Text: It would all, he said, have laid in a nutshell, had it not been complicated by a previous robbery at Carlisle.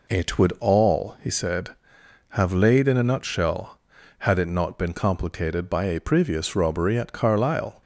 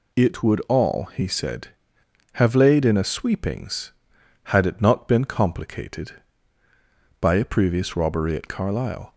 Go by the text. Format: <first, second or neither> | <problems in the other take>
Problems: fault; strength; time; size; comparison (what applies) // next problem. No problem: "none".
first | says "sweepings" for "nutshell"; at 3.0 s